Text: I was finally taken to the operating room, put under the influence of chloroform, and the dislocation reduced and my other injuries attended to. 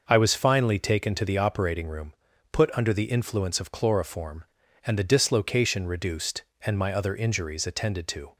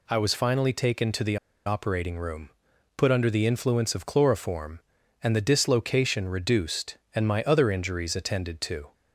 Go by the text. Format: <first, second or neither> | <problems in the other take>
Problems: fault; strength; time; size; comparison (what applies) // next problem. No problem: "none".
first | pauses between "the" and "operating"; slight; at 1.3 s; 0.28 s long